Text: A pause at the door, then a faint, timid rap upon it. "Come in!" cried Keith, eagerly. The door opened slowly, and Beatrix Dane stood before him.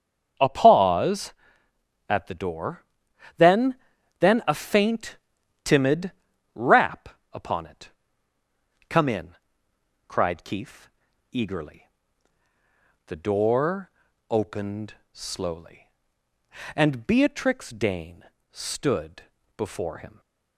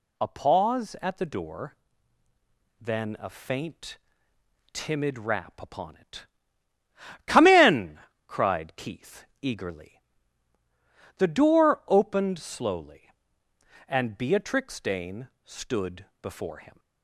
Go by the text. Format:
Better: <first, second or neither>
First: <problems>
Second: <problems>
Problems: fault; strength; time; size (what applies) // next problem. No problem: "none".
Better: second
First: starts louder than the rest; strong; until 2.1 s; 7 dB // says "then" twice; at 4.1 s // pauses between "timid" and "rap"; at 6.1 s; 0.42 s long // pauses between "rap" and "upon"; slight; at 7.0 s; 0.22 s long // pauses between "door" and "opened"; at 13.8 s; 0.38 s long // pauses between "opened" and "slowly"; slight; at 14.9 s; 0.18 s long // pauses between "Dane" and "stood"; slight; at 18.2 s; 0.26 s long // pauses between "stood" and "before"; slight; at 19.2 s; 0.34 s long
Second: pauses between "Dane" and "stood"; slight; at 15.2 s; 0.16 s long // pauses between "stood" and "before"; slight; at 16.0 s; 0.16 s long